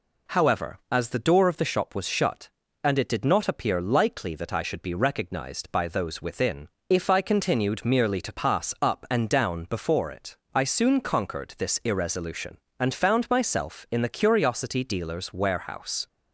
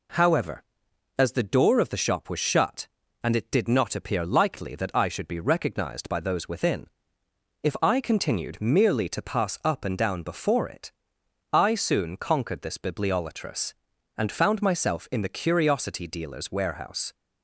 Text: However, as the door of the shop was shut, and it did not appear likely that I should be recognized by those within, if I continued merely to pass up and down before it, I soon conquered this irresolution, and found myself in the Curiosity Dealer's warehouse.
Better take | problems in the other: first | says "bibliolatrous" for "irresolution"; at 12.7 s

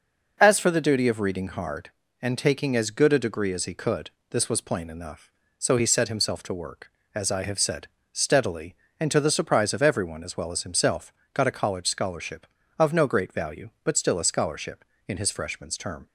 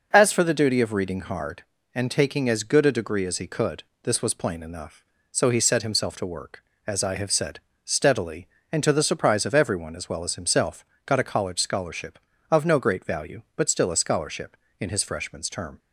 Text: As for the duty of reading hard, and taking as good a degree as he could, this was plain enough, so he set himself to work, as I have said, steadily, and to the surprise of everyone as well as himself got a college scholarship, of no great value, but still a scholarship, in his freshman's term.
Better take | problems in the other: neither | pauses between "himself" and "got"; slight; the same in both

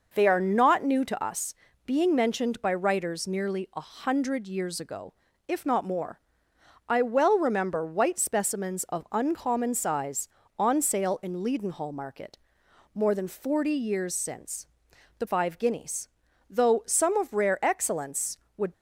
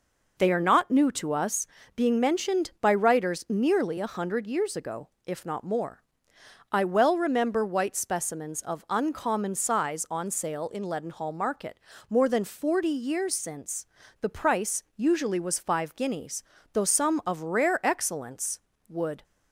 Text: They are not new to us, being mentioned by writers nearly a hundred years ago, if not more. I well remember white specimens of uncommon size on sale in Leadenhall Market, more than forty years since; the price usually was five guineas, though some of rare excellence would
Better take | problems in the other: second | skips "price usually was"; at 15.2 s

